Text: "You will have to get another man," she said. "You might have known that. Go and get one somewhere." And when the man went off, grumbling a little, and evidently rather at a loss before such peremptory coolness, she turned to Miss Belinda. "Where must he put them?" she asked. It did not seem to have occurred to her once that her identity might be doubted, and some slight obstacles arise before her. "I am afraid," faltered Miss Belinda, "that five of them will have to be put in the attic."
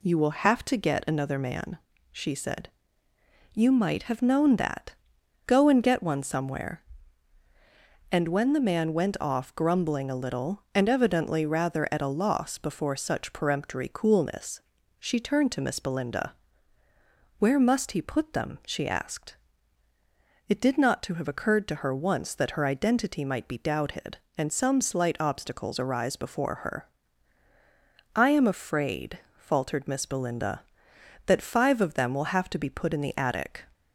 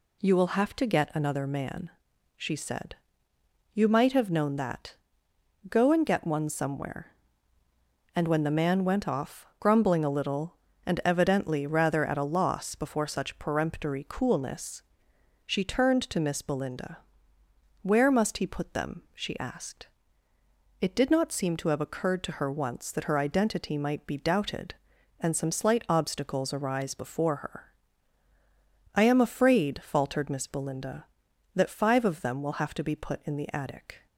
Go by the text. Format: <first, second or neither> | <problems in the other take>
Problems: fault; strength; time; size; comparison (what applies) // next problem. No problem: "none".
second | skips "seem"; at 21.0 s